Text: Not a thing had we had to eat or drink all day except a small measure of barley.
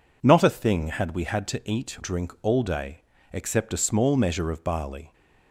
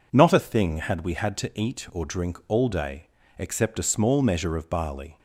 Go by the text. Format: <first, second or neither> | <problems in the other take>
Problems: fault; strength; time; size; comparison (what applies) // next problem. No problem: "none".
second | skips "or"; at 1.9 s // pauses between "day" and "except"; slight; at 3.0 s; 0.30 s long; slight in the second